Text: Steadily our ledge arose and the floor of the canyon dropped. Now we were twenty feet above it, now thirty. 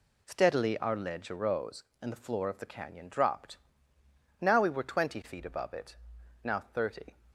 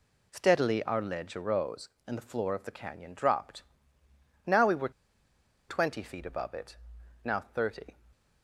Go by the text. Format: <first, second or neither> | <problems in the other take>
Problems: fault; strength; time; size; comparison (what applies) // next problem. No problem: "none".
first | pauses between "were" and "twenty"; noticeable; at 4.8 s; 0.79 s long